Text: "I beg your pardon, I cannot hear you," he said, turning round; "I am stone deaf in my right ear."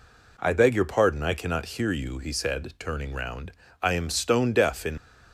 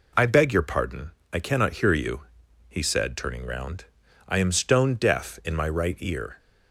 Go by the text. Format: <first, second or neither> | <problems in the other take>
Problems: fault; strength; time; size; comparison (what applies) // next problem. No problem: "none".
second | stops before "my right ear"; at 4.9 s